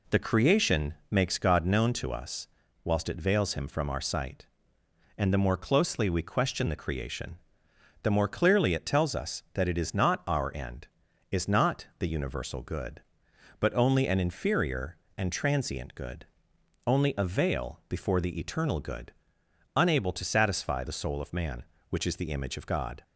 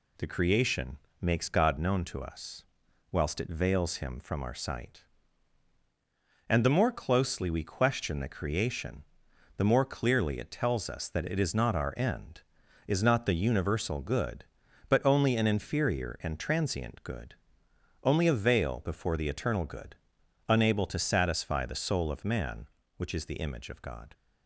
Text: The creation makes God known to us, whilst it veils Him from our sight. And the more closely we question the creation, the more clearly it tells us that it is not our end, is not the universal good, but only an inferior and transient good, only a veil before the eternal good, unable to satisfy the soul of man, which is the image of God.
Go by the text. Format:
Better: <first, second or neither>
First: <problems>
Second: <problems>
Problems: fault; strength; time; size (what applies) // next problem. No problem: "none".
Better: neither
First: pauses between "creation" and "makes"; slight; at 0.9 s; 0.16 s long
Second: pauses between "creation" and "makes"; slight; at 0.9 s; 0.22 s long